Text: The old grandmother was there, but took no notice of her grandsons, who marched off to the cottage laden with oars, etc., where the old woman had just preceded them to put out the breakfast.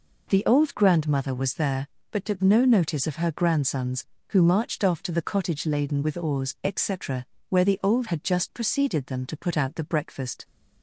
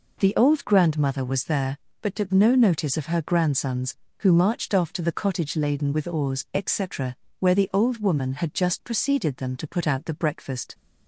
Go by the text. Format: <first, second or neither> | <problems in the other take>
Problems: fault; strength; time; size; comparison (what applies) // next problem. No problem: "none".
second | skips "woman"; at 8.0 s